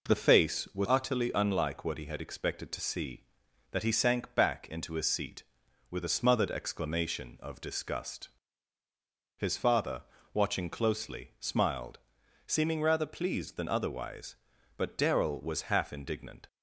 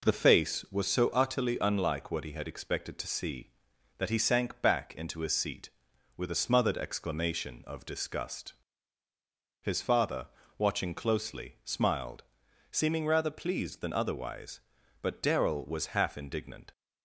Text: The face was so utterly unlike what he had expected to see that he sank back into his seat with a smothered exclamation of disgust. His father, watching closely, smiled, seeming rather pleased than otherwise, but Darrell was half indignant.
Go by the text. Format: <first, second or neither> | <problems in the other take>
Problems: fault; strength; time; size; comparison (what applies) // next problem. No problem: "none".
second | skips "so"; at 0.8 s